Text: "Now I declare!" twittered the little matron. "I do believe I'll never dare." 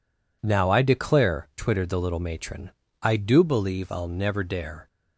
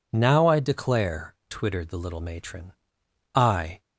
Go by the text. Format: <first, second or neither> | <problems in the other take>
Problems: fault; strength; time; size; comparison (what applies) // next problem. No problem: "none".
first | stops before "do believe I'll never dare"; at 3.7 s